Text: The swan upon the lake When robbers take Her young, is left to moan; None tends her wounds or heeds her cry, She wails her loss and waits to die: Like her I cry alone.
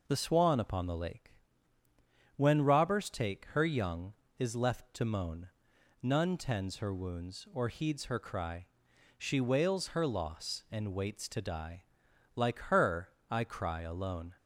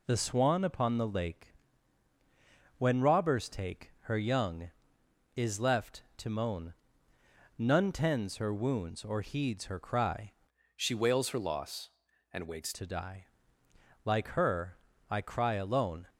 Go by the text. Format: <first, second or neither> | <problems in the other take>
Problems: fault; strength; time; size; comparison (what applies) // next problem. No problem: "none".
first | pauses between "lake" and "When"; at 1.5 s; 1.2 s long; also in the first // changes voice from "She" to "waits"; from 10.7 to 12.7 s; 2.0 s long // pauses between "her" and "I"; slight; at 14.7 s; 0.34 s long; slight in the first